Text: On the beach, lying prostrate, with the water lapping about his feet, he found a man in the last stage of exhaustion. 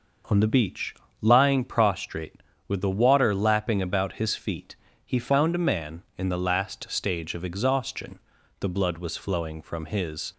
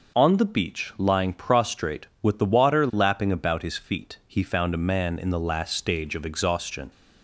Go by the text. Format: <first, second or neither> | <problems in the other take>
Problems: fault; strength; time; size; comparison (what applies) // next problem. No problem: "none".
second | goes on to say "The blood was flowing from his"; strong; from 8.6 s on; 1.7 s long